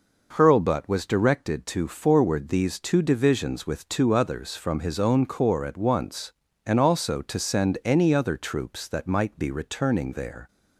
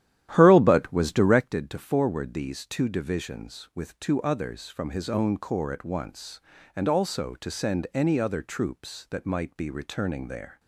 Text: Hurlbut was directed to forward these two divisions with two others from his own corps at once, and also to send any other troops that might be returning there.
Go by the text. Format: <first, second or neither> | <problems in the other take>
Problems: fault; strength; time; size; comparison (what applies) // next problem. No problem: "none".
first | starts louder than the rest; strong; until 1.6 s; 11.5 dB